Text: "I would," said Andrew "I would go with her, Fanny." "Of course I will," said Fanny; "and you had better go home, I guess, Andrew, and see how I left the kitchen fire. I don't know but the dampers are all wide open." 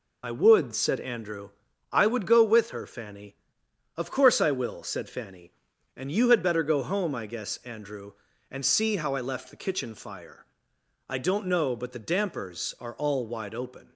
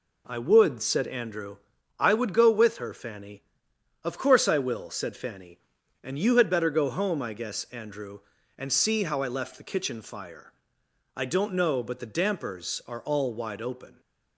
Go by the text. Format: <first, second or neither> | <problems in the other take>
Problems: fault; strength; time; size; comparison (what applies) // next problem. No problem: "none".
second | loses the start of "I"; at 0.2 s; 45 ms // pauses between "Andrew" and "I"; at 1.5 s; 0.42 s long; also in the second